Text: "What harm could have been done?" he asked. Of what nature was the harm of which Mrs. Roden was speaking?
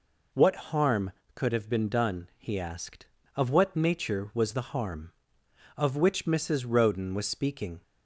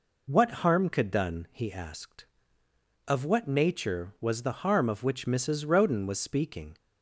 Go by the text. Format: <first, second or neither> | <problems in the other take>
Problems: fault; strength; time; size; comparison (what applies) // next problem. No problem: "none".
first | skips "have been"; at 1.1 s